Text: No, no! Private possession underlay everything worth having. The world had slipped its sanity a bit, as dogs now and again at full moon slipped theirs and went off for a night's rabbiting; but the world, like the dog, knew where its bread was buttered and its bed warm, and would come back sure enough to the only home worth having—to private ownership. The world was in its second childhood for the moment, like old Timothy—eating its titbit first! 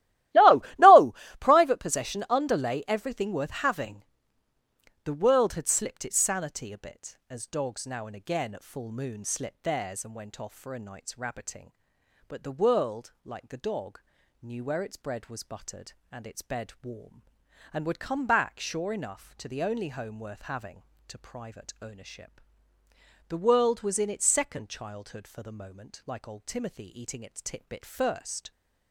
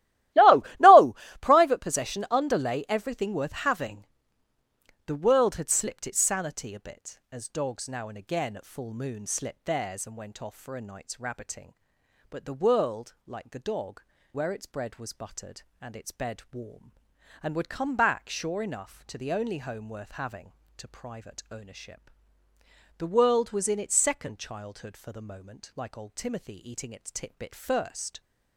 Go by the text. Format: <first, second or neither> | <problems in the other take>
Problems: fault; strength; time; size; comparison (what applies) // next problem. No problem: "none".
first | starts louder than the rest; strong; until 1.7 s; 15.5 dB; strong in the first // skips "knew"; at 14.1 s